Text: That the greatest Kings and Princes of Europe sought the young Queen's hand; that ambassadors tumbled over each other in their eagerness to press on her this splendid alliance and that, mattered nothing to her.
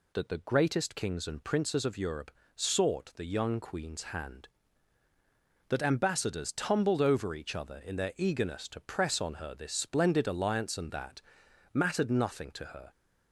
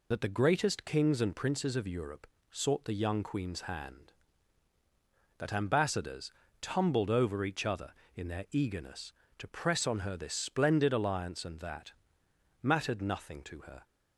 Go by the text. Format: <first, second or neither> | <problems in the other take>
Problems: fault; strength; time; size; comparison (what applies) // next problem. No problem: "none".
first | loses the start of "That"; at 0.1 s; 80 ms // pauses between "Europe" and "sought"; slight; at 2.2 s; 0.26 s long; slight in the first // pauses between "ambassadors" and "tumbled"; slight; at 6.2 s; 0.30 s long